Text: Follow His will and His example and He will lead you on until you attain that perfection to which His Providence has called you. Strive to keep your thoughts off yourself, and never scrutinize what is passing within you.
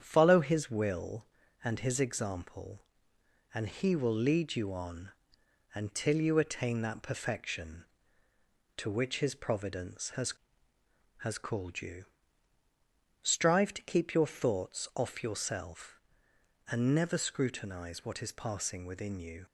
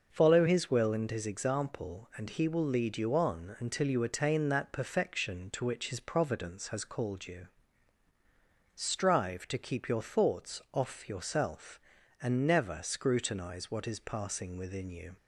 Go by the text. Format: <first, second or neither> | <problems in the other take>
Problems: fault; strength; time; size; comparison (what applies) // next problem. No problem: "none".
second | starts louder than the rest; strong; until 1.0 s; 8.5 dB // pauses between "on" and "until"; noticeable; at 5.0 s; 0.64 s long // says "has" twice; at 11.1 s